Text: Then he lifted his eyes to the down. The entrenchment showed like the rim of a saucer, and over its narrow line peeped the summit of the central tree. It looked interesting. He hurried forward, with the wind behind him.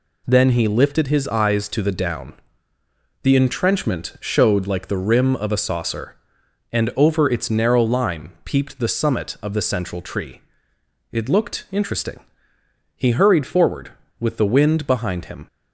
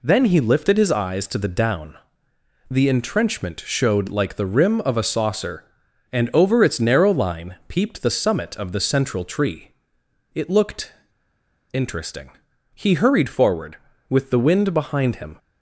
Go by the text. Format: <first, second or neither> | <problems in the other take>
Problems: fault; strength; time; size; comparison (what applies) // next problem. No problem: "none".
first | pauses between "looked" and "interesting"; noticeable; at 10.9 s; 0.79 s long